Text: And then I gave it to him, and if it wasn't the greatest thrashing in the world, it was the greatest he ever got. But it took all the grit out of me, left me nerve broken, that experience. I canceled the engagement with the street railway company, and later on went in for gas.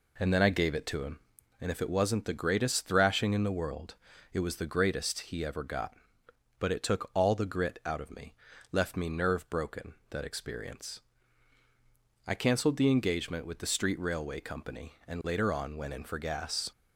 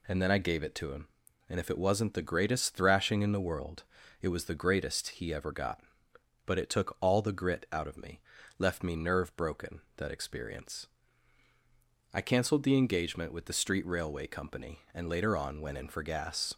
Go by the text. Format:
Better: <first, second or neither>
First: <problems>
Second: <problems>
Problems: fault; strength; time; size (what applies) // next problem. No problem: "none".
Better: second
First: starts louder than the rest; slight; until 1.8 s; 3 dB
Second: none